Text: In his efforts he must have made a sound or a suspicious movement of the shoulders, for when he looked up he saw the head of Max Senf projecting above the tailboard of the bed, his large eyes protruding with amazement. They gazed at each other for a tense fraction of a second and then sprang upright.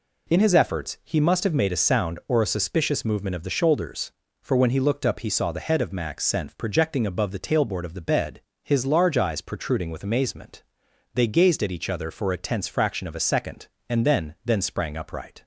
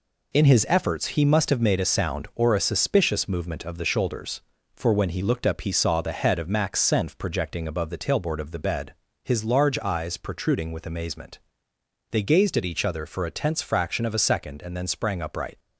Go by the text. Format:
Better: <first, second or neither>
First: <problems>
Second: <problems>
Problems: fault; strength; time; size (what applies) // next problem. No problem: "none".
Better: second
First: says "then" twice; at 14.4 s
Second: none